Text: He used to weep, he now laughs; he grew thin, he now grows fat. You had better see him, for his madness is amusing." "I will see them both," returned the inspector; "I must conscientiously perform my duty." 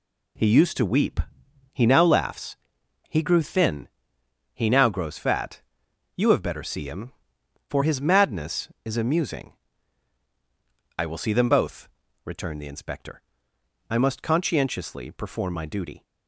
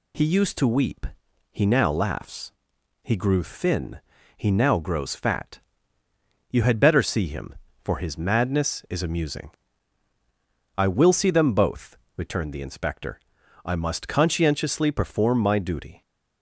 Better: second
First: says "have" for "had"; at 6.2 s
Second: none

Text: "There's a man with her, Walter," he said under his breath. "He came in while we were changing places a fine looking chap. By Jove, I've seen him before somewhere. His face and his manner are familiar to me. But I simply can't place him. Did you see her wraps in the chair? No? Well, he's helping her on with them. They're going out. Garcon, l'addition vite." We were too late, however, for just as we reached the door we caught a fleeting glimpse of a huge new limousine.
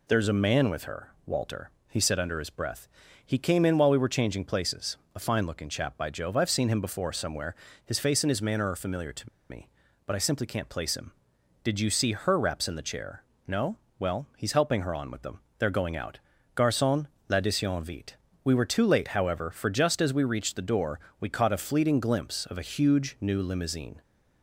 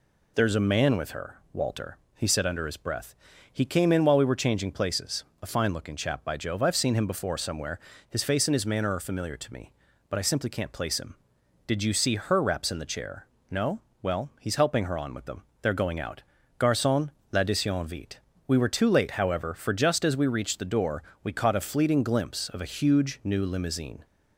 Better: second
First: pauses between "places" and "a"; slight; at 4.9 s; 0.18 s long // pauses between "to" and "me"; slight; at 9.2 s; 0.21 s long // pauses between "door" and "we"; slight; at 20.9 s; 0.20 s long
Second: pauses between "places" and "a"; slight; at 5.2 s; 0.18 s long // pauses between "door" and "we"; slight; at 21.0 s; 0.20 s long

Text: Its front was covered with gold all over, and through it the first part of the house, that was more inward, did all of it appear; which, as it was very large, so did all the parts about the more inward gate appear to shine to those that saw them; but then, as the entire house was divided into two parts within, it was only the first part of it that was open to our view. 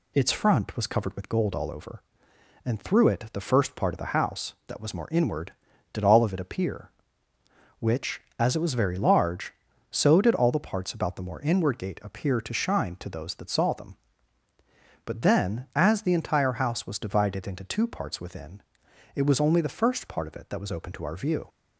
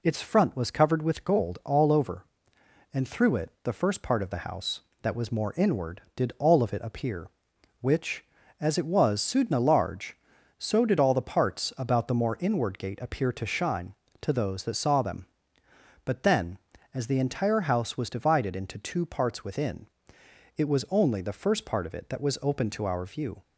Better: first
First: none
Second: says "sudna" for "very"; at 9.2 s

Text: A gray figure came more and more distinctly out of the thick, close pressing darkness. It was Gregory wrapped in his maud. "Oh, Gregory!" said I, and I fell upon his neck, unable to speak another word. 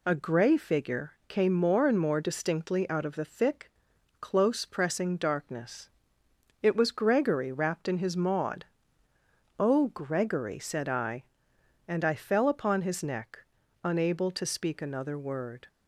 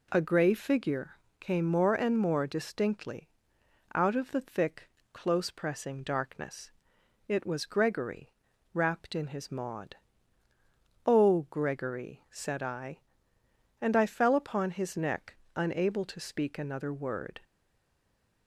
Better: first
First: pauses between "figure" and "came"; slight; at 1.1 s; 0.16 s long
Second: pauses between "figure" and "came"; slight; at 1.1 s; 0.22 s long // pauses between "distinctly" and "out"; noticeable; at 3.2 s; 0.66 s long // pauses between "Gregory" and "wrapped"; at 8.3 s; 0.42 s long // stays silent after the last word; from 17.4 s on; 1.0 s long

